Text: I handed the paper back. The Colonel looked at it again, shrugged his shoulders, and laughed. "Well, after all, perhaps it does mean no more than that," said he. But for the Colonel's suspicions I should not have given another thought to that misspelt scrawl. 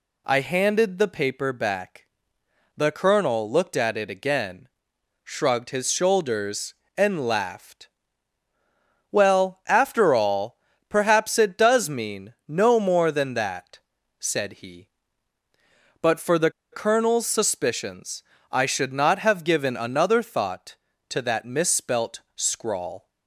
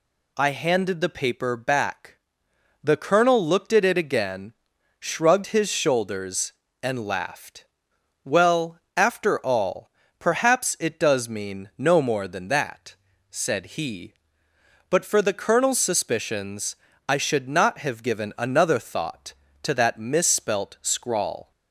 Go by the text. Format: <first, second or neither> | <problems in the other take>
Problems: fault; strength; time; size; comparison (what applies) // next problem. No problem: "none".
second | pauses between "the" and "Colonel's"; slight; at 16.5 s; 0.20 s long // pauses between "suspicions" and "I"; slight; at 18.2 s; 0.30 s long; slight in the second